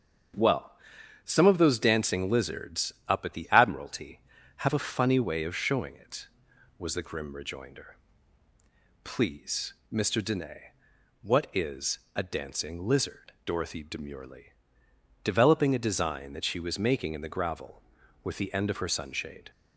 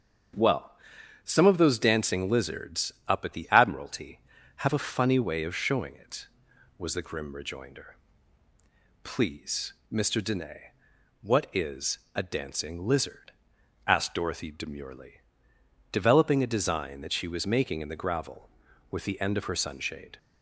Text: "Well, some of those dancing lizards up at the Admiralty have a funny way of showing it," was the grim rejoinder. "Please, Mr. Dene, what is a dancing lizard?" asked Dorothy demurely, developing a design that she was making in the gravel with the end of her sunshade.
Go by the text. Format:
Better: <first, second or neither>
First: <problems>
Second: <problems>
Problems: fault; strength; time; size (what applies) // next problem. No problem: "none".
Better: second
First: starts louder than the rest; until 1.8 s; 7 dB // pauses between "lizards" and "up"; slight; at 2.9 s; 0.16 s long // pauses between "is" and "a"; slight; at 11.9 s; 0.18 s long // skips "asked"; at 13.3 s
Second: starts louder than the rest; until 1.8 s; 7 dB // pauses between "lizards" and "up"; slight; at 2.9 s; 0.16 s long // pauses between "is" and "a"; slight; at 11.9 s; 0.18 s long